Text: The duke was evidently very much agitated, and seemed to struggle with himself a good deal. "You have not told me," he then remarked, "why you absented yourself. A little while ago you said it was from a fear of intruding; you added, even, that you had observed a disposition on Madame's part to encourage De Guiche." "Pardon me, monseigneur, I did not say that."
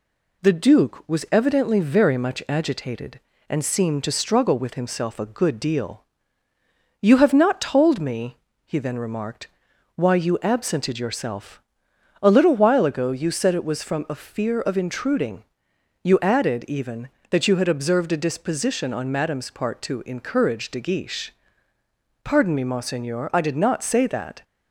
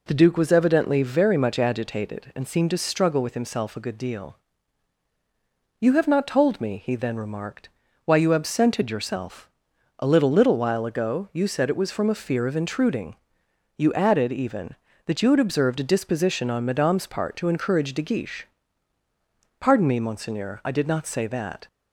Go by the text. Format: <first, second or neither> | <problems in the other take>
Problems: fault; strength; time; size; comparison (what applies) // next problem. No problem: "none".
first | says "little" twice; at 10.3 s